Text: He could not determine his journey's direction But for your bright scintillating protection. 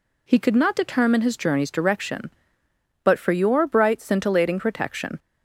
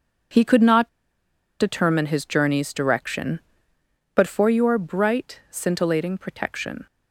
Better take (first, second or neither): first